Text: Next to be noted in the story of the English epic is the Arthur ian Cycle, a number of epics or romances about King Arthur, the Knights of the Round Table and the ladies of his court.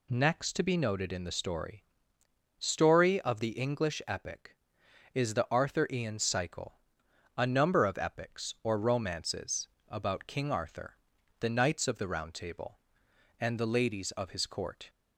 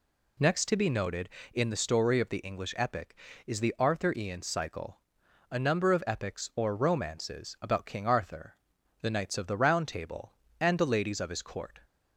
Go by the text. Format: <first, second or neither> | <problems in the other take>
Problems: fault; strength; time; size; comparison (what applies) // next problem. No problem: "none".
second | says "story" twice; at 2.5 s // pauses between "romances" and "about"; slight; at 9.6 s; 0.20 s long